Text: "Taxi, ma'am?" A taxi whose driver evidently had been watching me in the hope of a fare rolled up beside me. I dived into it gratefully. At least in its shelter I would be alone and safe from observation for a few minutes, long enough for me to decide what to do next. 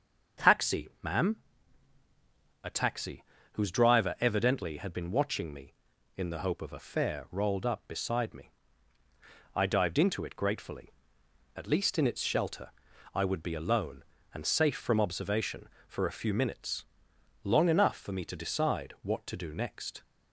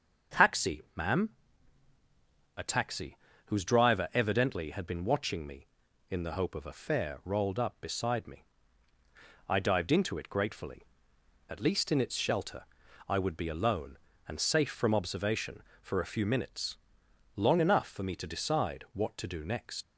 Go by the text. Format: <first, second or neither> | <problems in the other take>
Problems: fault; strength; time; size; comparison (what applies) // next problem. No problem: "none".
first | starts louder than the rest; until 2.7 s; 6.5 dB; also in the first // pauses between "taxi" and "whose"; slight; at 3.1 s; 0.30 s long; slight in the first // pauses between "shelter" and "I"; noticeable; at 12.6 s; 0.46 s long; noticeable in the first // leaves "next" unfinished; at 19.8 s; 95 ms